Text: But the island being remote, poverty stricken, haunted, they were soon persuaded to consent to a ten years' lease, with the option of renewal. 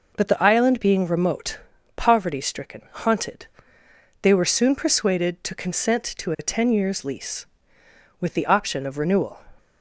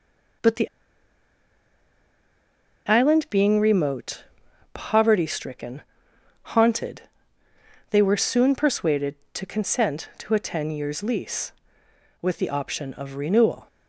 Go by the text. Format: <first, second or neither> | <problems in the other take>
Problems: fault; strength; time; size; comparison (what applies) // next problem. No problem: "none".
first | pauses between "the" and "island"; strong; at 0.6 s; 2.1 s long